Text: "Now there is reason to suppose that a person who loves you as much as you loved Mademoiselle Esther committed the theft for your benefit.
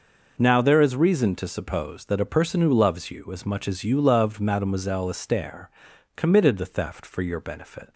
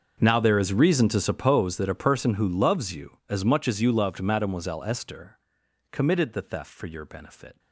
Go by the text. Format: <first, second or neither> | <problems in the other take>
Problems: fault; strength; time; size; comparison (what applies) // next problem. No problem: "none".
first | gets quieter; strong; throughout; 20 dB // pauses between "Esther" and "committed"; noticeable; at 5.3 s; 0.54 s long; noticeable in the first